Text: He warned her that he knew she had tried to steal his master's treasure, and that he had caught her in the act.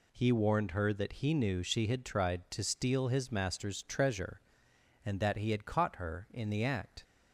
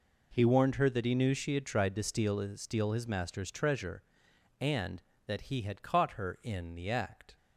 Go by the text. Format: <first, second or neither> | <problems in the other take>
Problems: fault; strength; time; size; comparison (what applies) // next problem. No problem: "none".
first | says "steal" twice; at 2.5 s